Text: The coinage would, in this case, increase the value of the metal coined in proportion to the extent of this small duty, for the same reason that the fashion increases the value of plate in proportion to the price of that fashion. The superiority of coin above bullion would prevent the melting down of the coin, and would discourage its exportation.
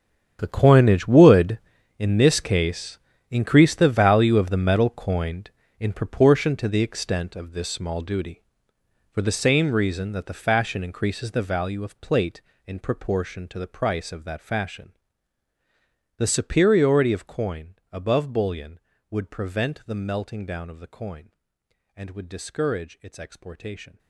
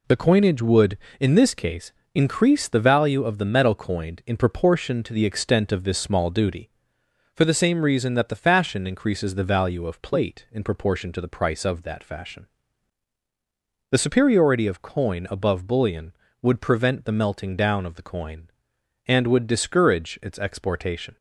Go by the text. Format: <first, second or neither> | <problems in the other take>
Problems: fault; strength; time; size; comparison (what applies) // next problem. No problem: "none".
second | gets quieter; strong; throughout; 16 dB // pauses between "coin" and "above"; slight; at 17.7 s; 0.18 s long